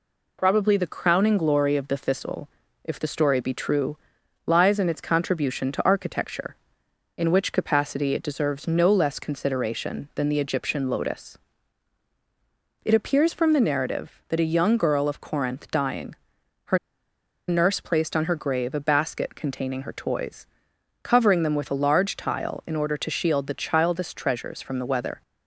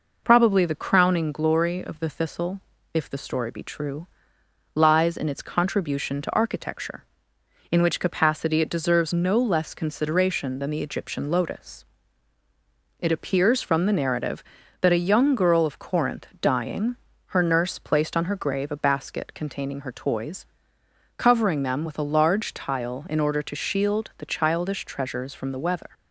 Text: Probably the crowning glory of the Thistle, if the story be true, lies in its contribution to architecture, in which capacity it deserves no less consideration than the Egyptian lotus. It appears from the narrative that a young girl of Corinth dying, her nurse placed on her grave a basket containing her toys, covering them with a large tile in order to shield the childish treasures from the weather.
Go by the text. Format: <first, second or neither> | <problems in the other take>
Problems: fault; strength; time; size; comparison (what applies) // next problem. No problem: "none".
second | pauses between "her" and "nurse"; noticeable; at 16.7 s; 0.70 s long